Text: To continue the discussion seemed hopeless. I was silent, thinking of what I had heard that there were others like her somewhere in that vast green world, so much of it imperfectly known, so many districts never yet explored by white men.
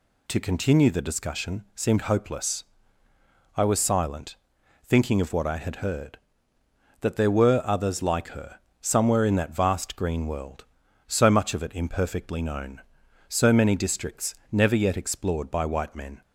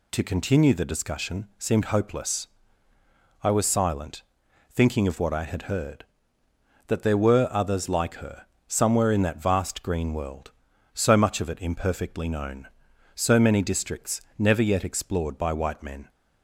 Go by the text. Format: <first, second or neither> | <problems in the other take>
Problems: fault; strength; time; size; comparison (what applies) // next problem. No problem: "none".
neither | pauses between "her" and "somewhere"; slight; the same in both // pauses between "districts" and "never"; slight; the same in both